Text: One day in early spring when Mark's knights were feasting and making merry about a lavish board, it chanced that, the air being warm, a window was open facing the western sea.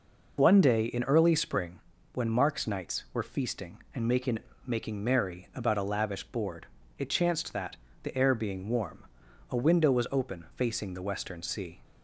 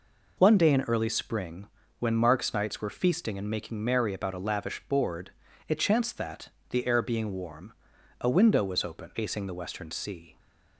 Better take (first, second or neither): second